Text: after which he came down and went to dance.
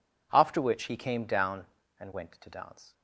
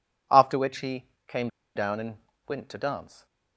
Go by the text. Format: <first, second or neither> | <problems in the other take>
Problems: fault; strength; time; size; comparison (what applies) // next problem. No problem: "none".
first | pauses between "he" and "came"; slight; at 1.0 s; 0.20 s long // pauses between "came" and "down"; slight; at 1.4 s; 0.27 s long // pauses between "and" and "went"; slight; at 2.1 s; 0.32 s long